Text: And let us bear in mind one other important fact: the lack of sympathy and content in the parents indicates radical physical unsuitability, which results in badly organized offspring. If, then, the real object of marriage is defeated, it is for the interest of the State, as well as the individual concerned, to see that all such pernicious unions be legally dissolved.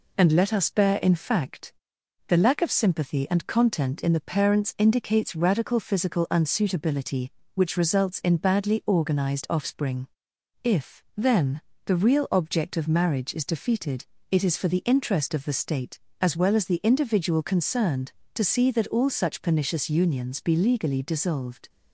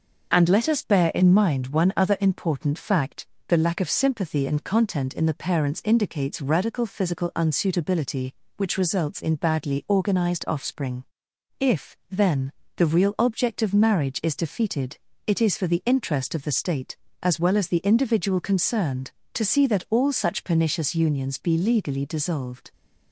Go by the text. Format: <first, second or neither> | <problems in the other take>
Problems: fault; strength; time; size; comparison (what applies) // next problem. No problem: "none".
second | skips "mind one other important"; at 1.1 s